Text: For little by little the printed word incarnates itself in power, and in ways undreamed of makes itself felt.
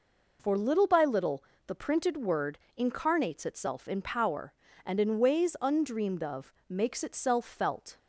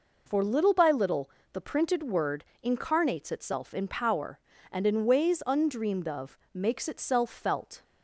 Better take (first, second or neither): neither